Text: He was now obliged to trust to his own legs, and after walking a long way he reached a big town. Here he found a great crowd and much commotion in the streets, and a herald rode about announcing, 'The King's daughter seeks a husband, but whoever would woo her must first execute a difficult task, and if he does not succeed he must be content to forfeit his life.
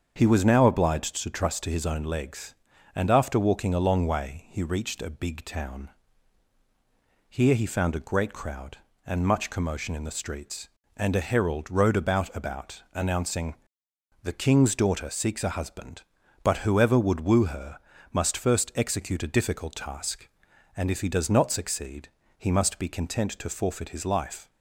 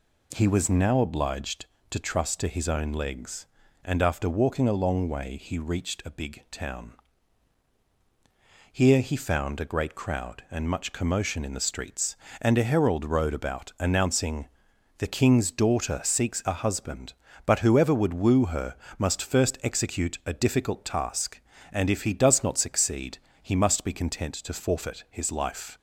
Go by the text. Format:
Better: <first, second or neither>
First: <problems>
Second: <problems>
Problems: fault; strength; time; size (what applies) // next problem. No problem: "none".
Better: second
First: starts louder than the rest; strong; until 1.1 s; 7 dB // says "about" twice; at 12.3 s // pauses between "her" and "must"; slight; at 17.7 s; 0.34 s long // pauses between "succeed" and "he"; slight; at 22.0 s; 0.30 s long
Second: pauses between "her" and "must"; slight; at 18.7 s; 0.20 s long // pauses between "succeed" and "he"; slight; at 23.1 s; 0.26 s long